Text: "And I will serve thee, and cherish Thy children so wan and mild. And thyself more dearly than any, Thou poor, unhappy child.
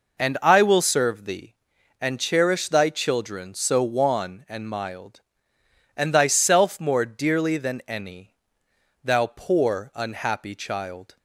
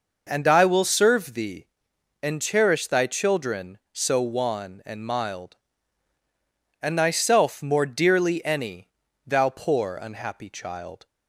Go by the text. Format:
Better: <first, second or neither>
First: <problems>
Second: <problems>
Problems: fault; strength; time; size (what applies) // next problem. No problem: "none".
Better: first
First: none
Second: skips "than"; at 8.4 s